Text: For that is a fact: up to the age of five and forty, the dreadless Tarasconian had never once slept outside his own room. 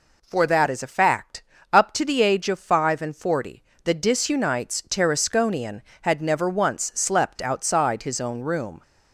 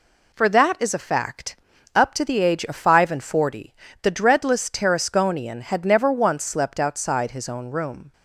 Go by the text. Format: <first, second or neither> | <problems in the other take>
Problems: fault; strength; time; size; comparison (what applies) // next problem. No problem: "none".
second | says "disunites" for "dreadless"; at 3.9 s